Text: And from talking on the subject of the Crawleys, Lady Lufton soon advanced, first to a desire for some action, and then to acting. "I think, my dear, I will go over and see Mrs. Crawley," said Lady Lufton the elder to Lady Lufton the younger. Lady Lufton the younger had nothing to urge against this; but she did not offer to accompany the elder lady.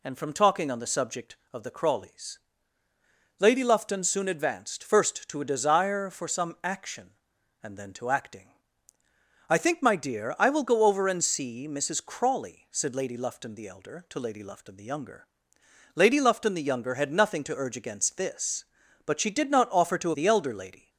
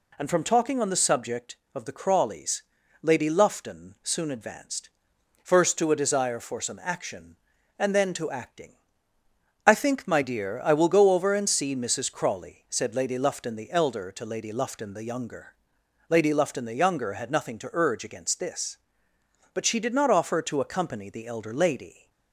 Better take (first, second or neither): second